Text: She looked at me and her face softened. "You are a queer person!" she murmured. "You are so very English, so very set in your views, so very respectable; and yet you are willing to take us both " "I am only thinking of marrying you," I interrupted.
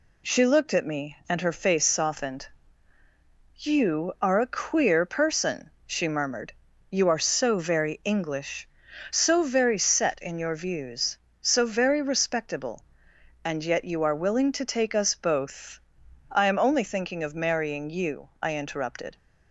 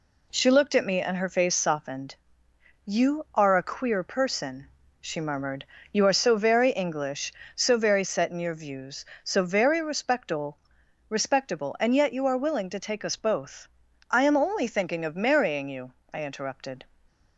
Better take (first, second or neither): first